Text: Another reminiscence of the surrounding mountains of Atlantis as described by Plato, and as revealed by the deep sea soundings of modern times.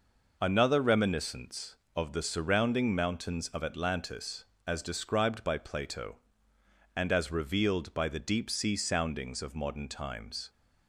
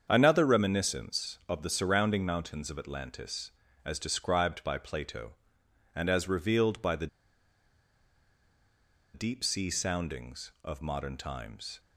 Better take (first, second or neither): first